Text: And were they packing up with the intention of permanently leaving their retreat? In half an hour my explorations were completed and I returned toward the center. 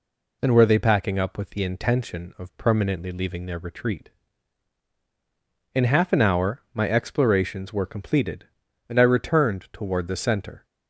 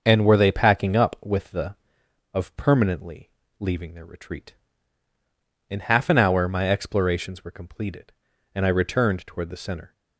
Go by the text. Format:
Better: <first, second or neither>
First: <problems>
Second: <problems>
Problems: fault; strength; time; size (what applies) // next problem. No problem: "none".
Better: first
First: none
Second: starts louder than the rest; until 1.0 s; 6.5 dB // skips "intention"; at 2.0 s // pauses between "permanently" and "leaving"; slight; at 3.2 s; 0.30 s long